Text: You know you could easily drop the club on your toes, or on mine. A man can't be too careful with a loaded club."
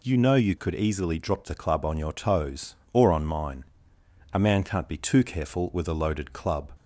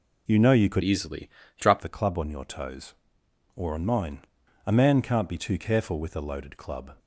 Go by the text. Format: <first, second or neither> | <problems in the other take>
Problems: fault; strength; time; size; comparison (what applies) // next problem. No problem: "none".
first | changes voice from "easily" to "drop"; from 0.8 to 1.8 s; 1.0 s long // pauses between "easily" and "drop"; slight; at 1.2 s; 0.30 s long